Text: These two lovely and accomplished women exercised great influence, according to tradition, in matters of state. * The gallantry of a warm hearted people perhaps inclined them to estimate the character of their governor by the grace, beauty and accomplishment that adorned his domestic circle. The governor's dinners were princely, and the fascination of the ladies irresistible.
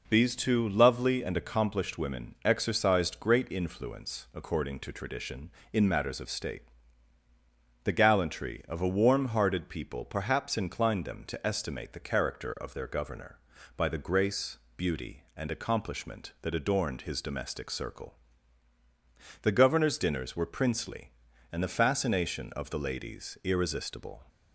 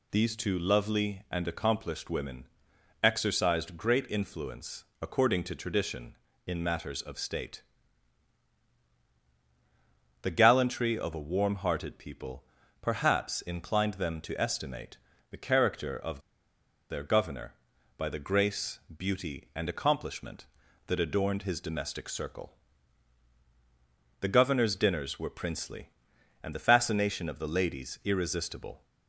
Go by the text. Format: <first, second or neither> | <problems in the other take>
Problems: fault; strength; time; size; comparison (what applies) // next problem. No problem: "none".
first | pauses between "women" and "exercised"; noticeable; at 2.4 s; 0.56 s long // pauses between "people" and "perhaps"; at 12.4 s; 0.38 s long // pauses between "estimate" and "the"; slight; at 14.9 s; 0.34 s long // pauses between "of" and "their"; noticeable; at 16.1 s; 0.70 s long